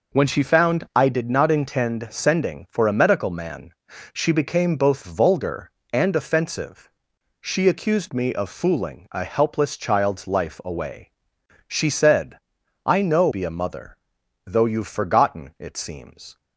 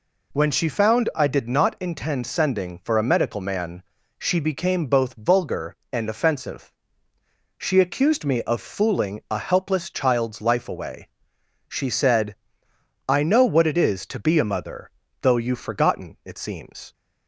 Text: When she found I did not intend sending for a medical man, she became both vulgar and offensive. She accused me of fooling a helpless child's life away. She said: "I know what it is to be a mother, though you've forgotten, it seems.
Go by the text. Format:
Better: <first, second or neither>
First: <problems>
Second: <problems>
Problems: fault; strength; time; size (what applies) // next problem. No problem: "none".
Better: second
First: skips "what it is to"; at 13.2 s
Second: none